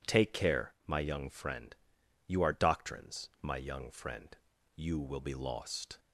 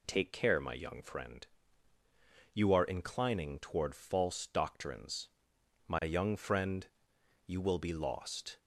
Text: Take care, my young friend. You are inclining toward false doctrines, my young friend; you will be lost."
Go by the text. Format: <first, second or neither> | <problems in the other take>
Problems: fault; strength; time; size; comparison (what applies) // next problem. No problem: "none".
second | skips "inclining toward false"; at 2.5 s